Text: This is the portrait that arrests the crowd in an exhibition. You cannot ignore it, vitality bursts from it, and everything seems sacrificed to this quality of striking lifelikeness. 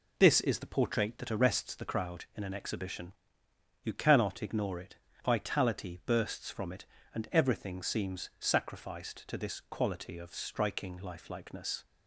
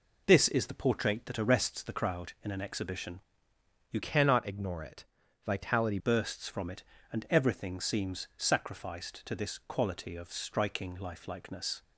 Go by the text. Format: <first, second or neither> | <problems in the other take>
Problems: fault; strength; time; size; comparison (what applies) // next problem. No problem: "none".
first | changes voice from "cannot" to "vitality"; from 4.0 to 5.9 s; 1.9 s long